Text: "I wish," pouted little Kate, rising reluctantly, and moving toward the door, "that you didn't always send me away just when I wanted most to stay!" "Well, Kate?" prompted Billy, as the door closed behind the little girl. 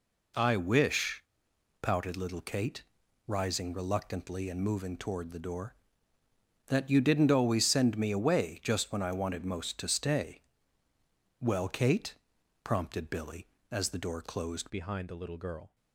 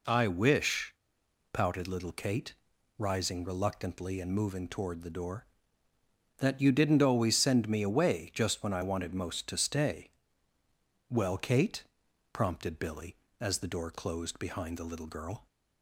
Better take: second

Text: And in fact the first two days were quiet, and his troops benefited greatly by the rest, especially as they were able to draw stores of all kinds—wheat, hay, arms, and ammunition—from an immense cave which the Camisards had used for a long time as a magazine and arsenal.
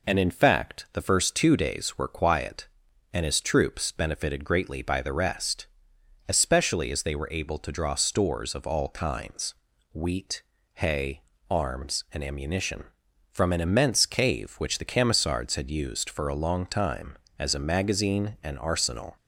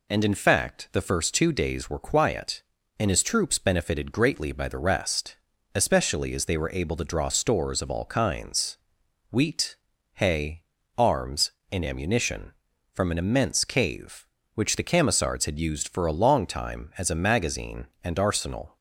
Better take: neither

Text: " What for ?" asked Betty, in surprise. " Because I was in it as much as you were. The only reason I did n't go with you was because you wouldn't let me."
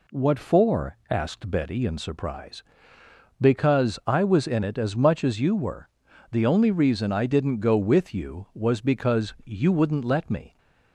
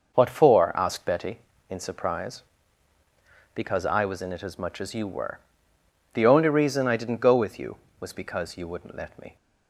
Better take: first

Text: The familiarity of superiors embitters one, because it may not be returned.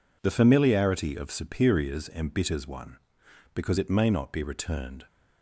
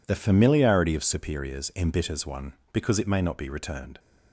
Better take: neither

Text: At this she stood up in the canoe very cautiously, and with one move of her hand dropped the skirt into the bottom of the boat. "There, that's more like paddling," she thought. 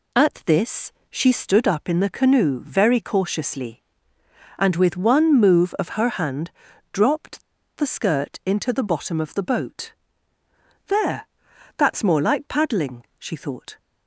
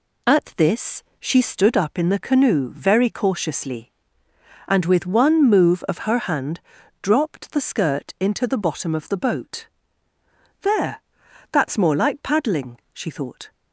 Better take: second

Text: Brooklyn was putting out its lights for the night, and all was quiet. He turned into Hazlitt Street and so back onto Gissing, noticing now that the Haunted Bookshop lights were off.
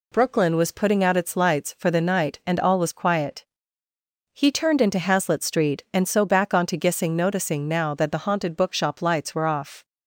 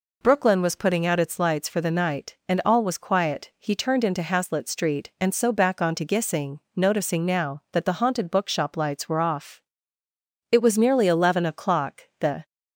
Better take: first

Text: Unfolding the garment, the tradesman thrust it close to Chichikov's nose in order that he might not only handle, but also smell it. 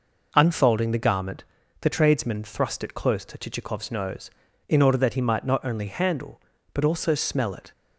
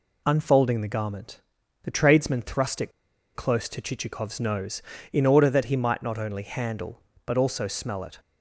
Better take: first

